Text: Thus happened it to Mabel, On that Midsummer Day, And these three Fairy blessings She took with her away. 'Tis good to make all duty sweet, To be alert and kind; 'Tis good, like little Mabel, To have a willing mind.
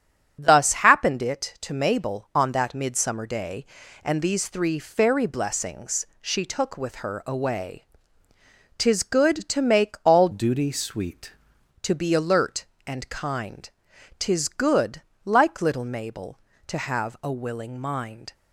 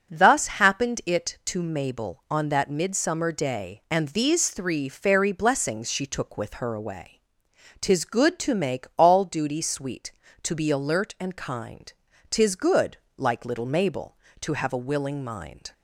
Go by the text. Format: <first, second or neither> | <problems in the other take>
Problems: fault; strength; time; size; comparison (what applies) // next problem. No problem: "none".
second | starts louder than the rest; until 1.4 s; 7 dB; also in the second // pauses between "blessings" and "She"; slight; at 6.0 s; 0.16 s long // changes voice from "duty" to "sweet"; from 10.3 to 11.3 s; 1.0 s long